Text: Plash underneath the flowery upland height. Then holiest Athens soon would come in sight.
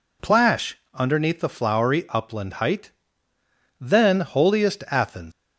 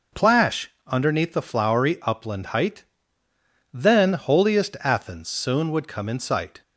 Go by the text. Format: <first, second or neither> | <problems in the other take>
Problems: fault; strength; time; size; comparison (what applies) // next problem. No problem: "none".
second | pauses between "Plash" and "underneath"; slight; at 0.7 s; 0.16 s long; slight in the second // stops before "soon would come in sight"; at 5.3 s